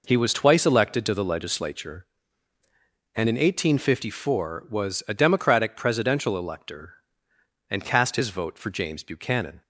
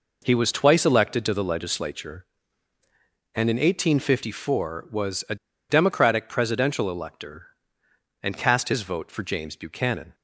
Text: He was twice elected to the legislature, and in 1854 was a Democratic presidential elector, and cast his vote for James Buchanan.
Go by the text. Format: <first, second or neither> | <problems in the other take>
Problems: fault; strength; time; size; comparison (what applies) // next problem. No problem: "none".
first | pauses between "a" and "Democratic"; slight; at 5.3 s; 0.34 s long